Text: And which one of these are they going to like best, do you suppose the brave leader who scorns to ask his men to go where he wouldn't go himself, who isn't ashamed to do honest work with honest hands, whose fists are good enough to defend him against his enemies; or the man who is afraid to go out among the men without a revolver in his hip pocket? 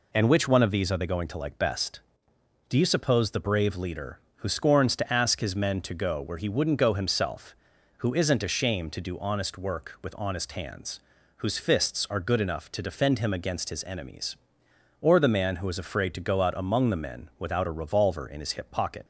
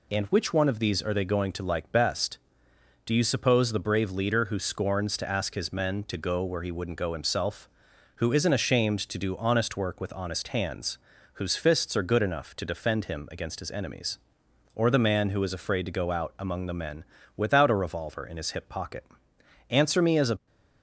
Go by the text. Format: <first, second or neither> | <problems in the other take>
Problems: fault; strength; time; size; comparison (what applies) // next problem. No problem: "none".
first | pauses between "men" and "without"; slight; at 17.0 s; 0.32 s long // goes on to say "Answer me as a"; noticeable; from 19.6 s on; 0.76 s long